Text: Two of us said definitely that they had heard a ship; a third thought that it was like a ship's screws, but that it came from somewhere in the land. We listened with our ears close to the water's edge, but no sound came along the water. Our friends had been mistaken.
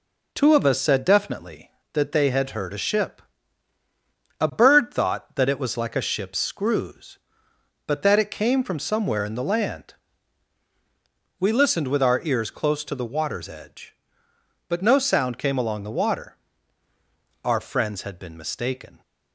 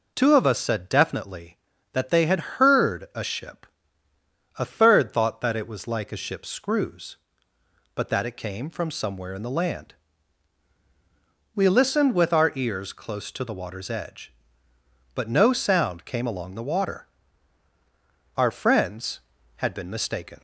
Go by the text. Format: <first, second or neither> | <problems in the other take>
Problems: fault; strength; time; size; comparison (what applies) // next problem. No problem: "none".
second | says "bird" for "third"; at 4.5 s